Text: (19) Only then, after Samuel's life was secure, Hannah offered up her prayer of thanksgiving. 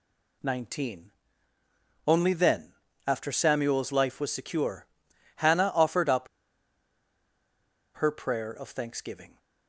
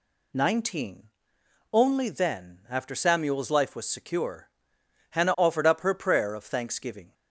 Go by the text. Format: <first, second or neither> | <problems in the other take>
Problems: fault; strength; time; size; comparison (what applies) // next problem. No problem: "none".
second | pauses between "up" and "her"; strong; at 6.2 s; 1.6 s long